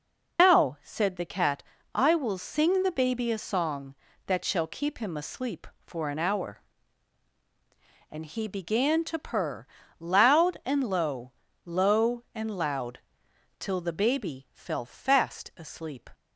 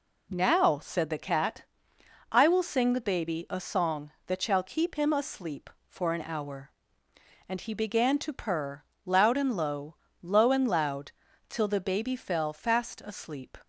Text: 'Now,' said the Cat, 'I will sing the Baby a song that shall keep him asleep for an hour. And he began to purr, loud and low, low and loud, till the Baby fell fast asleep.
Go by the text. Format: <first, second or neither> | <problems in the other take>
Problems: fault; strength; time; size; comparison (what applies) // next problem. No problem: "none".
second | loses the start of "Now"; at 0.3 s; 130 ms